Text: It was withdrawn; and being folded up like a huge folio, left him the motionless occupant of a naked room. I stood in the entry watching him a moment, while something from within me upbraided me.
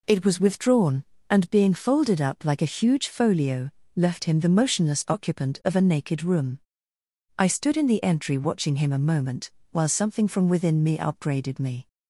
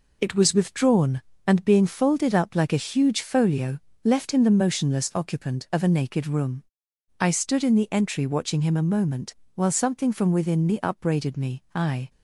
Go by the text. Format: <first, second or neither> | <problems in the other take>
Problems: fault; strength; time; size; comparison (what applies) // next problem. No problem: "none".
first | goes on to say "I"; slight; from 11.7 s on; 0.34 s long